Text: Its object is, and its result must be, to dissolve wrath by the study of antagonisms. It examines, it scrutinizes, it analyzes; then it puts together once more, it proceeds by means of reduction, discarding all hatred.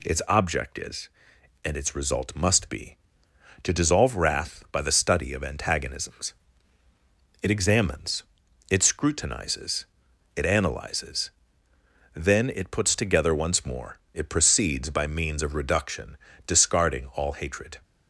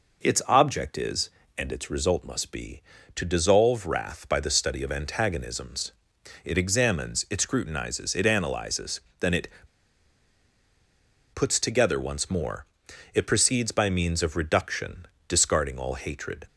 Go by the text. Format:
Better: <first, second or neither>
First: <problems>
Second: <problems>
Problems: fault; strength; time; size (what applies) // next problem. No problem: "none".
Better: first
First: none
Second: pauses between "it" and "puts"; strong; at 9.4 s; 1.8 s long